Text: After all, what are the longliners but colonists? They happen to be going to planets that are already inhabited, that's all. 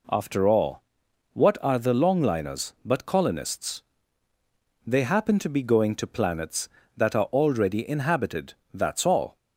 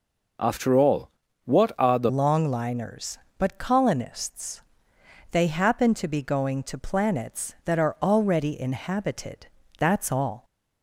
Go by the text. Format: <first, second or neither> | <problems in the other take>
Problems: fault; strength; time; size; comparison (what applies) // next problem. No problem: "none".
first | changes voice at "longliners"; from 2.0 s on; 8.4 s long